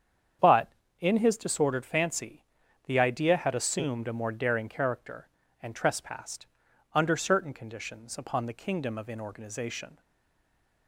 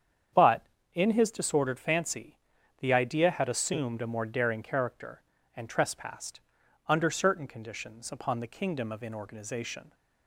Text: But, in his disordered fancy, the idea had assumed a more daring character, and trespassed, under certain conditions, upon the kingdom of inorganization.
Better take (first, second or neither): second